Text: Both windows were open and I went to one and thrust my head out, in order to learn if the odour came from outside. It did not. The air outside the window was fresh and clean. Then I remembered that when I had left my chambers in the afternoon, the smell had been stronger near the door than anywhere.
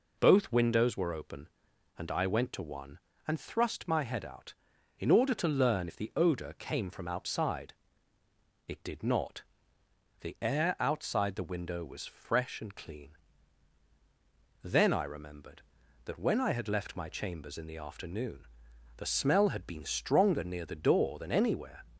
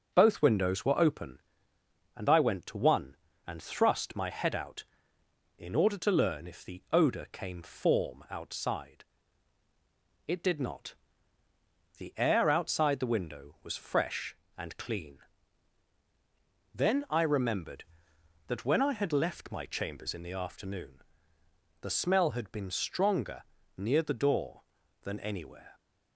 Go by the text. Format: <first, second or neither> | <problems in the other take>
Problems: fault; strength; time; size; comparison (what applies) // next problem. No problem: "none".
first | says "form" for "from"; at 7.6 s // pauses between "stronger" and "near"; slight; at 23.4 s; 0.36 s long